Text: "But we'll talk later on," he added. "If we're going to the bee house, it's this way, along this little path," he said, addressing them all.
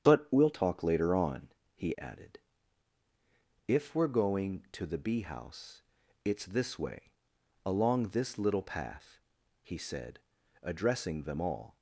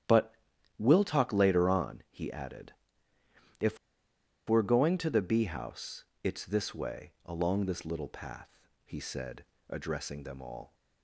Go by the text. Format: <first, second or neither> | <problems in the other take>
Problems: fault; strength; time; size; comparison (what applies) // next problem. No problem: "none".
first | starts louder than the rest; strong; until 1.4 s; 10 dB; strong in the first // pauses between "But" and "we'll"; at 0.3 s; 0.42 s long // pauses between "If" and "we're"; noticeable; at 3.7 s; 0.72 s long